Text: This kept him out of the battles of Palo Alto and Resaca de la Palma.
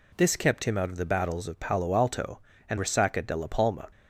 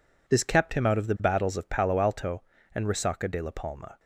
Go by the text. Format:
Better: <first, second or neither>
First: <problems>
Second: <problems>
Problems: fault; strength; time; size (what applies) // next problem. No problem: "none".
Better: neither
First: none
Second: none